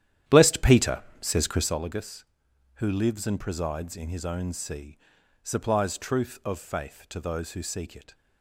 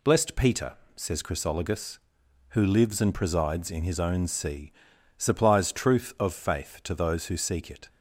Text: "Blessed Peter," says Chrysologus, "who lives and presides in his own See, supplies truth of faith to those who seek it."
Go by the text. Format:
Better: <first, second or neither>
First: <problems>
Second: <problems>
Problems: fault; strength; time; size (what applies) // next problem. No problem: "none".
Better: second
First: starts louder than the rest; strong; until 1.8 s; 11 dB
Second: none